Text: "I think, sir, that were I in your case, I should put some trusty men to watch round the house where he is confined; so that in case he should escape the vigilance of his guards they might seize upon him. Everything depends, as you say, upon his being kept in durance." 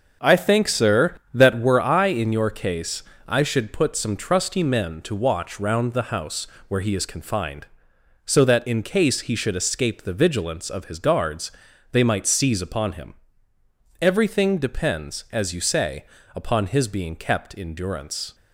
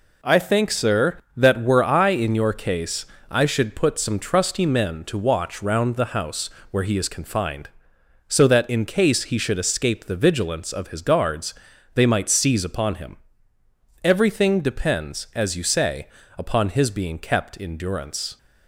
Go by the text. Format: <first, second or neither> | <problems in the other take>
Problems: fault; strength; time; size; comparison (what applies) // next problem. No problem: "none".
second | starts louder than the rest; noticeable; until 1.7 s; 6 dB // pauses between "house" and "where"; slight; at 6.4 s; 0.22 s long; slight in the second // pauses between "guards" and "they"; at 11.5 s; 0.40 s long; also in the second